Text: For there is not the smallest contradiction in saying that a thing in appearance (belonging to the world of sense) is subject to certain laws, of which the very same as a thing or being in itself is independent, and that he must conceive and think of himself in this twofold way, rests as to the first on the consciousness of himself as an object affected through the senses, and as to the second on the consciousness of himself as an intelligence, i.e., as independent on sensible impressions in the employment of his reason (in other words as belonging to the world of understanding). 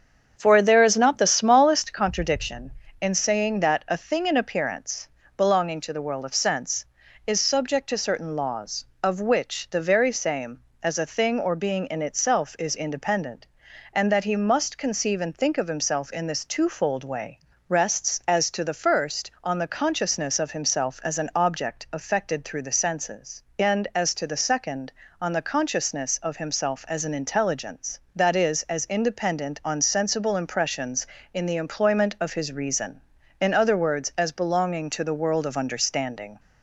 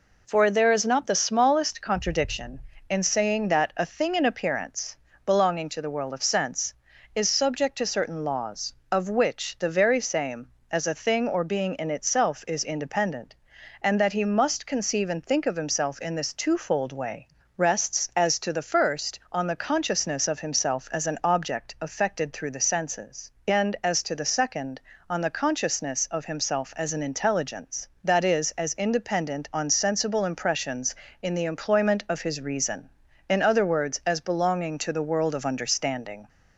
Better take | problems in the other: second | starts louder than the rest; strong; until 2.2 s; 7.5 dB

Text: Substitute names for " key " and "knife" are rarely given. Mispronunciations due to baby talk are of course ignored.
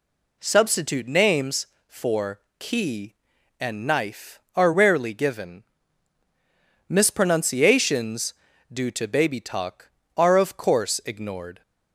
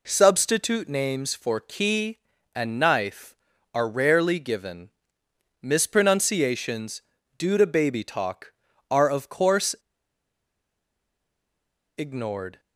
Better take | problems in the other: first | pauses between "Mispronunciations" and "due"; slight; at 7.0 s; 0.36 s long; also in the first // pauses between "course" and "ignored"; strong; at 9.7 s; 2.2 s long

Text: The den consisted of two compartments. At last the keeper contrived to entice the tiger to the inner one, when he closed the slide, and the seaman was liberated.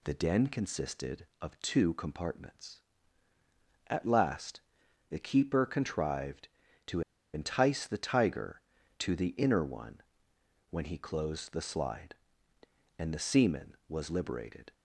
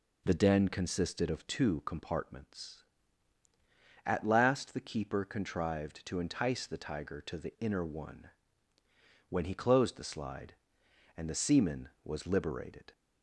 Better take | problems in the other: second | pauses between "last" and "the"; noticeable; at 4.6 s; 0.50 s long // pauses between "to" and "entice"; slight; at 7.0 s; 0.33 s long

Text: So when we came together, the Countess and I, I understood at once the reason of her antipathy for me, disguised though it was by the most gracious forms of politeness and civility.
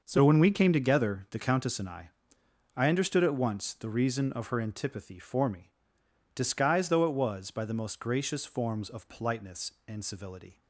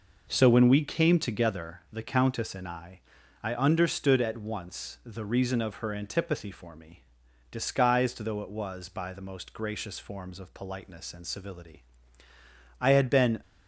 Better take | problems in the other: first | goes on to say "I had been"; noticeable; from 12.7 s on; 0.62 s long

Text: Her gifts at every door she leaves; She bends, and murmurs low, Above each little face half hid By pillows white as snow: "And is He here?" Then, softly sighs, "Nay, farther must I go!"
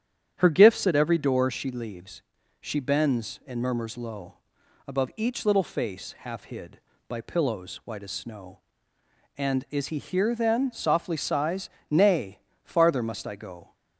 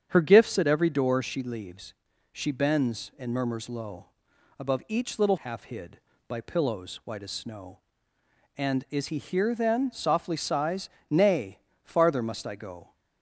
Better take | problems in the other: first | starts louder than the rest; strong; until 1.1 s; 8 dB; strong in the first // skips "face"; at 5.3 s

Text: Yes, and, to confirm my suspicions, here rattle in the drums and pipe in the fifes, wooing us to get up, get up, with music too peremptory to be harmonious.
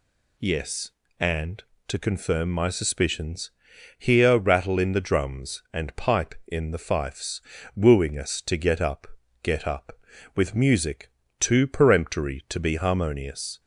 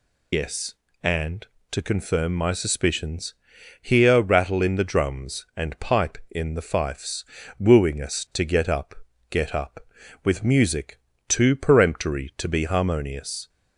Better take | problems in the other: first | loses the start of "Yes"; at 0.3 s; 100 ms // pauses between "music" and "too"; slight; at 10.9 s; 0.30 s long; slight in the first

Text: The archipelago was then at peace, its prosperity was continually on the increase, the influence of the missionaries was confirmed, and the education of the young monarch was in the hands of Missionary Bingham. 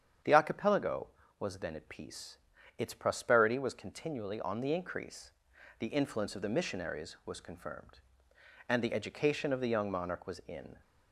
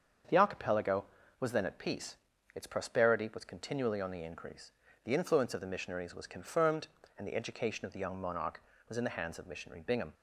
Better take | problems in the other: second | starts louder than the rest; strong; until 1.5 s; 8 dB; also in the second // stops before "the hands of Missionary Bingham"; at 10.8 s

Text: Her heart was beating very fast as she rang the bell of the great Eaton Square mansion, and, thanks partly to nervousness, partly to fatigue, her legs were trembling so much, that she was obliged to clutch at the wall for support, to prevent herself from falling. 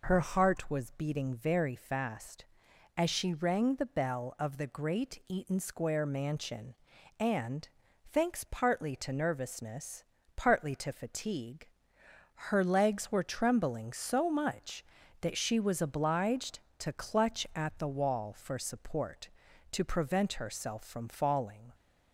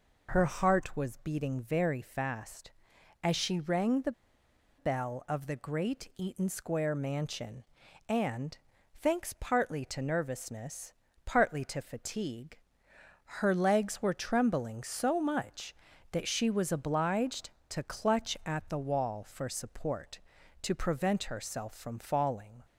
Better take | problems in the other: first | pauses between "the" and "bell"; noticeable; at 4.1 s; 0.66 s long

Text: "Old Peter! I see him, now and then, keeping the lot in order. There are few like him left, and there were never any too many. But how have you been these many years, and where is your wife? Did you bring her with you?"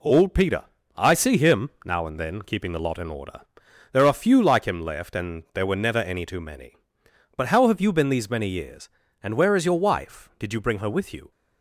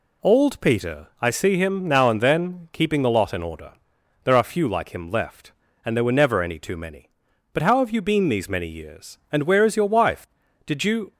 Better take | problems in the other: first | stops before "bring her with you"; at 11.1 s

